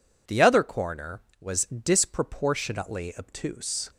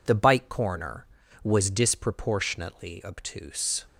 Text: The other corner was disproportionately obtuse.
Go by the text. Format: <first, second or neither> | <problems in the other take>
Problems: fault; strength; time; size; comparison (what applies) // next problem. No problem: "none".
first | says "bike" for "other"; at 0.1 s